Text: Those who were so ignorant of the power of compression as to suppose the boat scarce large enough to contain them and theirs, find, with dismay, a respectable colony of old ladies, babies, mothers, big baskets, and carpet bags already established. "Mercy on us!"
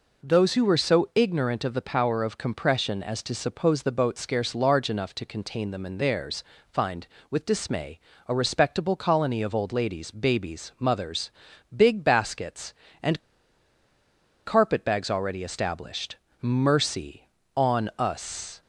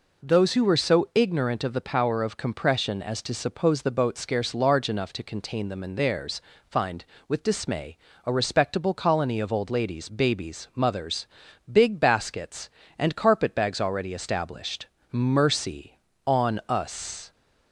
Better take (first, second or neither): second